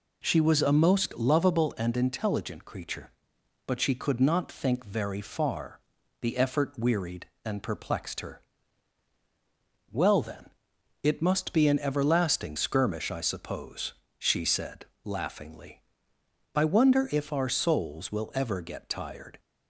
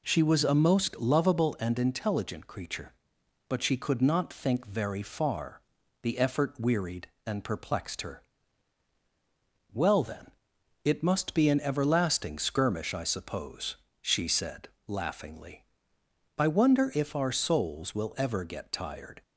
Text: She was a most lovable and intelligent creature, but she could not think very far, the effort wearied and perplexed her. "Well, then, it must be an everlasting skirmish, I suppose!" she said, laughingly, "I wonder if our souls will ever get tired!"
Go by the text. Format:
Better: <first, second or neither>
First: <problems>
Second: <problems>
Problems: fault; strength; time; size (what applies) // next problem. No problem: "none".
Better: neither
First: none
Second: none